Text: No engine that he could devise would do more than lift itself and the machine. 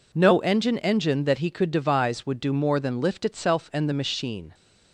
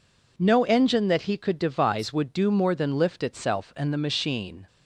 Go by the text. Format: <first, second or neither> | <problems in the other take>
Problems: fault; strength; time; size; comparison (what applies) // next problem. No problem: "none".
second | says "engine" twice; at 0.7 s